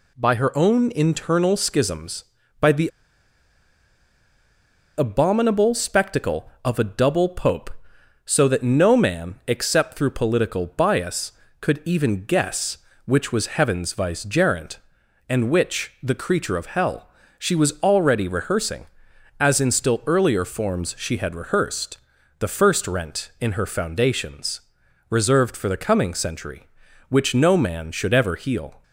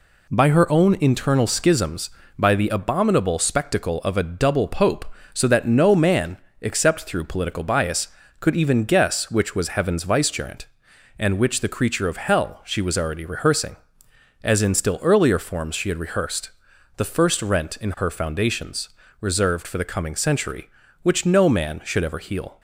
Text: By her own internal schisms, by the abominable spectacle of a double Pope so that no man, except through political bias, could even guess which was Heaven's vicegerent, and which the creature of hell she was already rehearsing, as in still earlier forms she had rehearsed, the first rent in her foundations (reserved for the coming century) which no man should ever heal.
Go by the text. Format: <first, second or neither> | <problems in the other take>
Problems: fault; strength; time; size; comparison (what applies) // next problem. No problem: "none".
second | pauses between "the" and "abominable"; strong; at 2.8 s; 2.1 s long // pauses between "hell" and "she"; slight; at 17.0 s; 0.30 s long